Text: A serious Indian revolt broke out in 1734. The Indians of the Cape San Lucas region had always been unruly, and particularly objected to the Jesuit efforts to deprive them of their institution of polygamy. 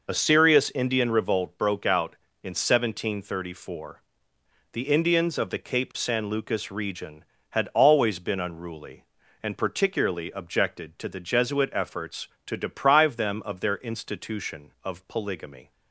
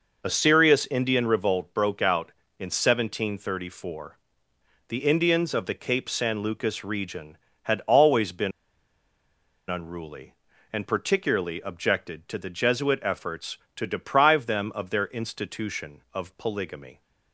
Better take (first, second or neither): first